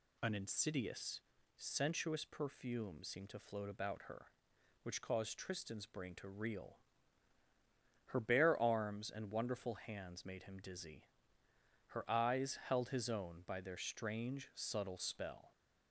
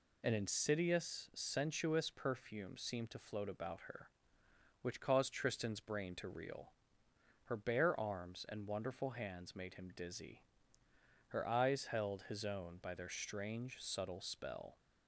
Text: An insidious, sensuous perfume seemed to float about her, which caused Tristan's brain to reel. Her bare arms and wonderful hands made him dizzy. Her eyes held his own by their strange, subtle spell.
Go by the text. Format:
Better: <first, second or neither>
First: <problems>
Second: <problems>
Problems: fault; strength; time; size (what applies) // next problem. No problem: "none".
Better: neither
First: none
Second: none